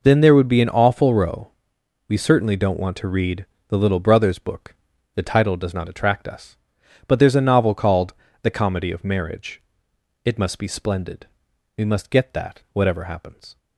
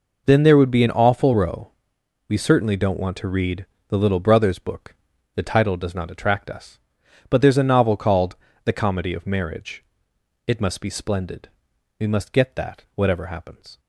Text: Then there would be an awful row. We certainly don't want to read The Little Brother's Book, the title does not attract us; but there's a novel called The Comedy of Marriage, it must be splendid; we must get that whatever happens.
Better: neither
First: pauses between "read" and "The"; slight; at 3.4 s; 0.22 s long // pauses between "called" and "The"; slight; at 8.1 s; 0.28 s long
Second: pauses between "read" and "The"; slight; at 3.6 s; 0.22 s long // pauses between "called" and "The"; slight; at 8.3 s; 0.28 s long

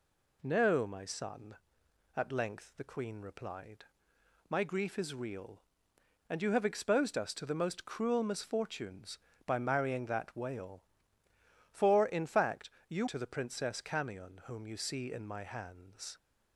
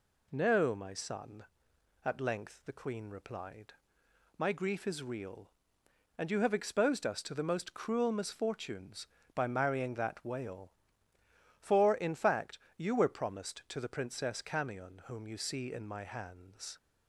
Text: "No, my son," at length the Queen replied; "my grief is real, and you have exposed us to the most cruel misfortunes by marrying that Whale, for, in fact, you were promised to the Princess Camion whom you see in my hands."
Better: second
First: skips "were promised"; at 13.0 s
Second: none

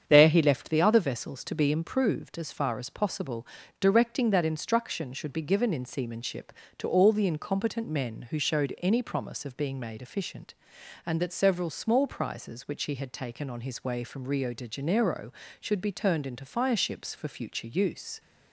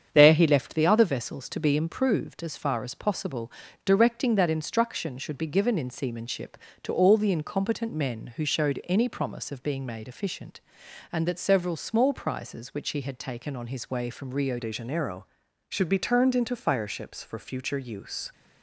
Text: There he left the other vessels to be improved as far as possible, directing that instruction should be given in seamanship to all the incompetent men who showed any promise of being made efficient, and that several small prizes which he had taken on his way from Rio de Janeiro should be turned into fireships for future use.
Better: first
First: starts louder than the rest; strong; until 1.0 s; 8 dB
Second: starts louder than the rest; strong; until 1.1 s; 8 dB // changes voice at "de"; from 14.5 s on; 3.8 s long

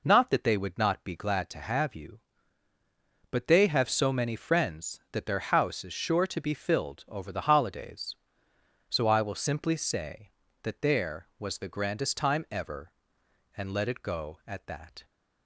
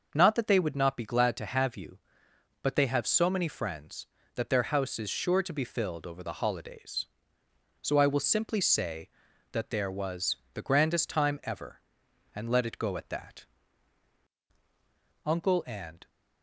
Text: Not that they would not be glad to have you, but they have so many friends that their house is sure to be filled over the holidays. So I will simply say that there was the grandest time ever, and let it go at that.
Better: first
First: none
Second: starts louder than the rest; noticeable; until 1.1 s; 6 dB // pauses between "was" and "the"; slight; at 10.3 s; 0.18 s long // goes on to say "Uncle and"; noticeable; from 15.2 s on; 0.84 s long

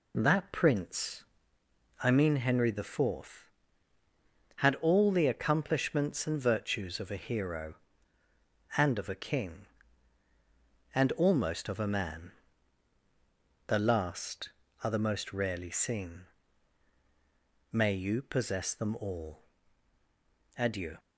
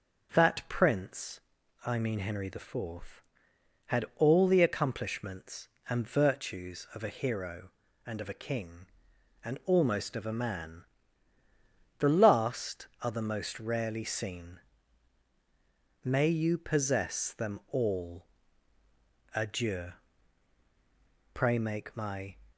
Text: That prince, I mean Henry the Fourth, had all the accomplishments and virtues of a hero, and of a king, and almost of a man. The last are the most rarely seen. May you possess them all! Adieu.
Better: first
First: none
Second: starts louder than the rest; until 1.8 s; 7 dB // goes on to say "Pray make my"; noticeable; from 21.3 s on; 1.0 s long

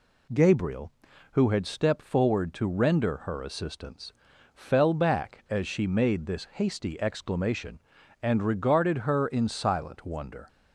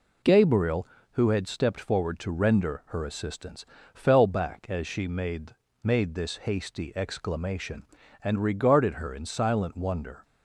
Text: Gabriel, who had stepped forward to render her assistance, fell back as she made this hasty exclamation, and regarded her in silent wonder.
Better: first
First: none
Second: says "made" twice; at 5.8 s

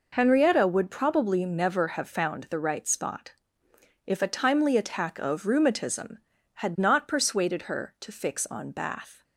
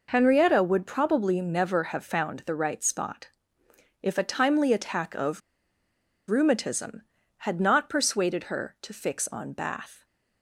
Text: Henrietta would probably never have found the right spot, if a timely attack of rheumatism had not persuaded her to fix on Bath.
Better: first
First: none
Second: pauses between "of" and "rheumatism"; noticeable; at 5.4 s; 0.90 s long

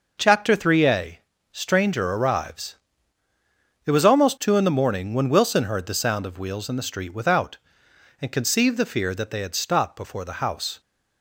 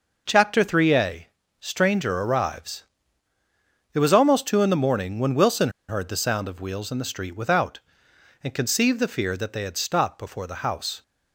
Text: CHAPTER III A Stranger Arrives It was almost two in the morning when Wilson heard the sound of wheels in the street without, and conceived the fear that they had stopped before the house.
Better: first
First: pauses between "A" and "Stranger"; slight; at 1.1 s; 0.32 s long // pauses between "Arrives" and "It"; at 2.7 s; 1.1 s long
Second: pauses between "A" and "Stranger"; slight; at 1.2 s; 0.32 s long // pauses between "Arrives" and "It"; at 2.8 s; 1.1 s long // pauses between "Wilson" and "heard"; slight; at 5.6 s; 0.19 s long

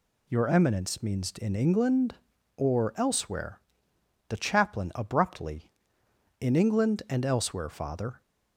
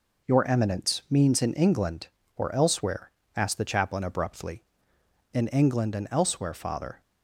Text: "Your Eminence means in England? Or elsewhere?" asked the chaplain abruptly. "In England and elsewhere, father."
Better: second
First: skips "asked"; at 3.9 s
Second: none

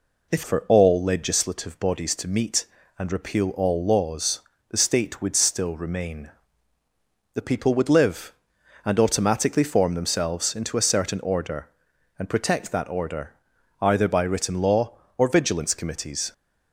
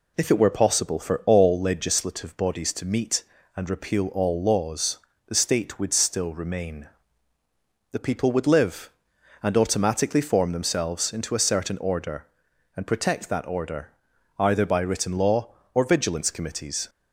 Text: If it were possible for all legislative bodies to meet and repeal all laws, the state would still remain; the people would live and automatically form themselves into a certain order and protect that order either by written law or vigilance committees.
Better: second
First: skips "it were possible"; at 0.4 s // pauses between "order" and "either"; noticeable; at 13.3 s; 0.48 s long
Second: pauses between "order" and "either"; noticeable; at 13.9 s; 0.48 s long

